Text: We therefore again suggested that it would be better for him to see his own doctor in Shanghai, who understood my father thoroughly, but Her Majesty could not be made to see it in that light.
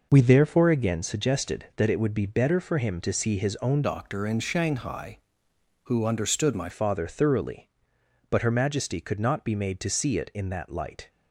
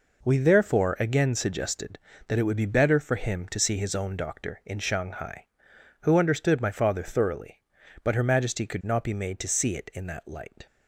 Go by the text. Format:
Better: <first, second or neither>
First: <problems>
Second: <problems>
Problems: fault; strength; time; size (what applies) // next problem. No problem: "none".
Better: second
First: changes voice from "doctor" to "my"; from 3.8 to 6.6 s; 2.8 s long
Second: none